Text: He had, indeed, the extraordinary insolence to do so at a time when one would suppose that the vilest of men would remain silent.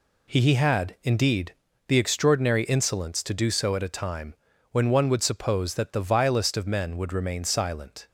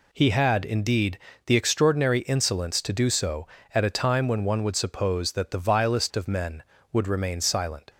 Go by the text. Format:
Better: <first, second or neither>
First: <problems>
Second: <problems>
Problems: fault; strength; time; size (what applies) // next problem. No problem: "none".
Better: second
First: says "He" twice; at 0.4 s // pauses between "time" and "when"; at 4.3 s; 0.38 s long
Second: none